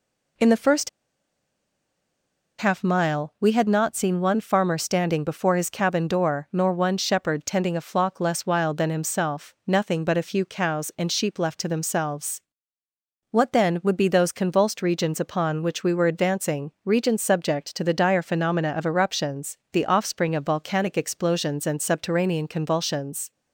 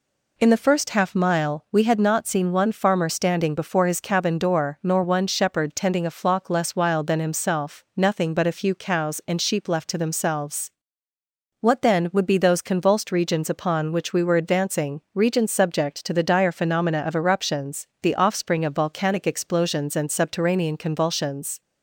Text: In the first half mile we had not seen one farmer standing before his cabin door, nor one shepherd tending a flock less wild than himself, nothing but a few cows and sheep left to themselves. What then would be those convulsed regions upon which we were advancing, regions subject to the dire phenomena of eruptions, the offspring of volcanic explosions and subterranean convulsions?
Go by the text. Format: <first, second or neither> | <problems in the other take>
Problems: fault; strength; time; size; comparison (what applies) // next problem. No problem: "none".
second | pauses between "first" and "half"; strong; at 0.8 s; 1.6 s long